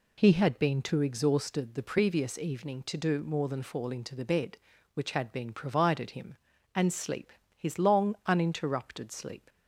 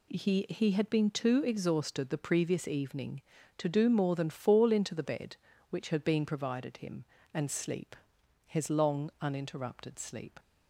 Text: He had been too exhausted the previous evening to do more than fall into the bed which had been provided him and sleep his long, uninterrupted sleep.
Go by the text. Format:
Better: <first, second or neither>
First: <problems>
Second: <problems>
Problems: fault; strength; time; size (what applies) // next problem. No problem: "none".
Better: first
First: pauses between "sleep" and "his"; slight; at 7.3 s; 0.24 s long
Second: says "He" twice; at 0.4 s // pauses between "sleep" and "his"; noticeable; at 7.9 s; 0.52 s long